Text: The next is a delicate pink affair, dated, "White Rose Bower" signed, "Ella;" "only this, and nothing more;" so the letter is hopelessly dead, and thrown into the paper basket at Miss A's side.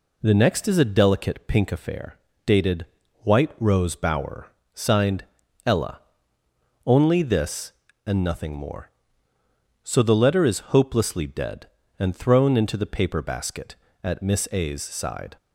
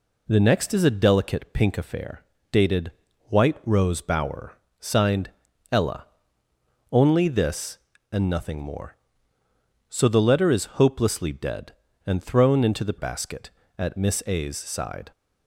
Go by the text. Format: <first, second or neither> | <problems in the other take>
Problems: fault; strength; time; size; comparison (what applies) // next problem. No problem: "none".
first | pauses between "Bower" and "signed"; slight; at 4.5 s; 0.26 s long; slight in the first // skips "paper"; at 12.9 s